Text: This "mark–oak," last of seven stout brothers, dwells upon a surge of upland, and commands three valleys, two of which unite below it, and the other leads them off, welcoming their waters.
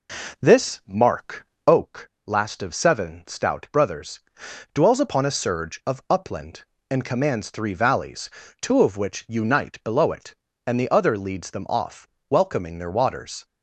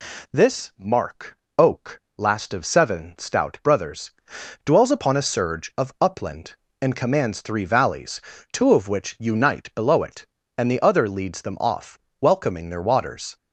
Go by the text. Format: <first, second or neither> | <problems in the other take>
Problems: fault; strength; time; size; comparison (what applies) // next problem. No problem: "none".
second | starts louder than the rest; noticeable; until 1.8 s; 4.5 dB